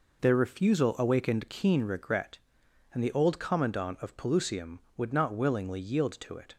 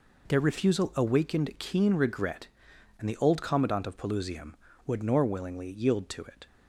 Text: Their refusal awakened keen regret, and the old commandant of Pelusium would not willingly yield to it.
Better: first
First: none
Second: says "nor" for "not"; at 5.0 s

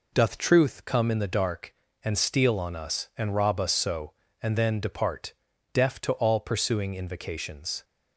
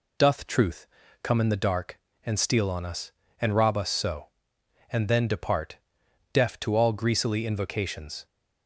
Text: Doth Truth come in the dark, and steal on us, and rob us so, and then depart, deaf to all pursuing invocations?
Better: first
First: none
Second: pauses between "Truth" and "come"; slight; at 0.8 s; 0.36 s long // says "greasily" for "pursuing"; at 6.9 s

